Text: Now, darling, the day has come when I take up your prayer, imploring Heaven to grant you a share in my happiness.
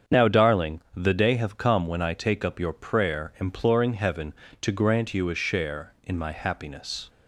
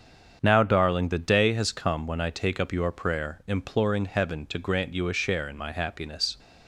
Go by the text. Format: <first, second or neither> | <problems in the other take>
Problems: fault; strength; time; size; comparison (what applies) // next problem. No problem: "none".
second | starts louder than the rest; strong; until 1.2 s; 7 dB; strong in the second // says "have" for "has"; at 1.3 s